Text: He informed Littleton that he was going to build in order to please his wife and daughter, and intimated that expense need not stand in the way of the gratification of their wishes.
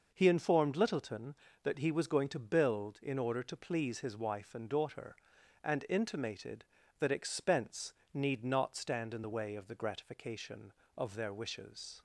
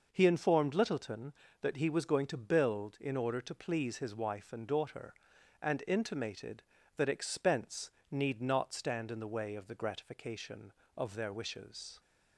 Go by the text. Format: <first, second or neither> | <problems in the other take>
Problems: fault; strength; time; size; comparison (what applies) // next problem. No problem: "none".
neither | pauses between "expense" and "need"; slight; the same in both